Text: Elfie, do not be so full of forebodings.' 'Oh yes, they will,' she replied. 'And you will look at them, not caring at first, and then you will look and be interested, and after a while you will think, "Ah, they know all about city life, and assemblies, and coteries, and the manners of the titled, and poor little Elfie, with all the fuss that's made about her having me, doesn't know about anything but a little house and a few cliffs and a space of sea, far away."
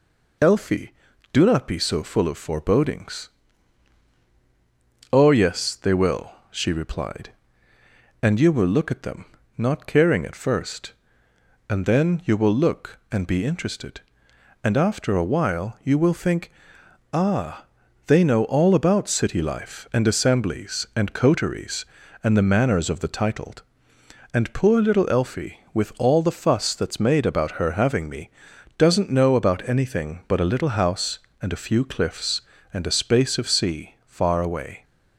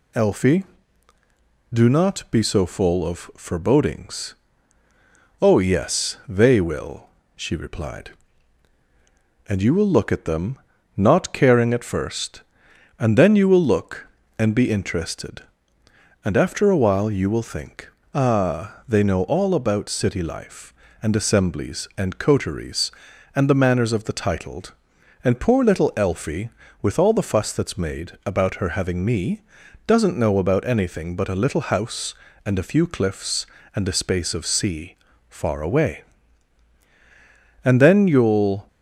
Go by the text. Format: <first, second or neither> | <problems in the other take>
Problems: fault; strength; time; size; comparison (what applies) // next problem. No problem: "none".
first | goes on to say "And then you'll"; noticeable; from 37.6 s on; 1.0 s long